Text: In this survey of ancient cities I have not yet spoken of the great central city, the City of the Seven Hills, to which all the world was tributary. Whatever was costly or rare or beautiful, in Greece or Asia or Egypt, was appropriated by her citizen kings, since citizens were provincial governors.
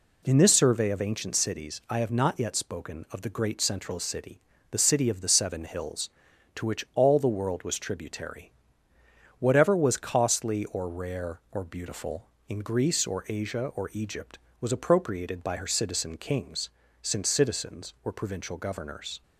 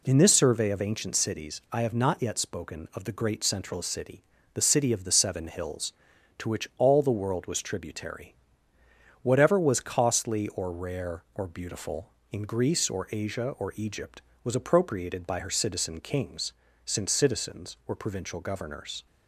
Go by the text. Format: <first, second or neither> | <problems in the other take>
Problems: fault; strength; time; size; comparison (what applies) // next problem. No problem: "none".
neither | none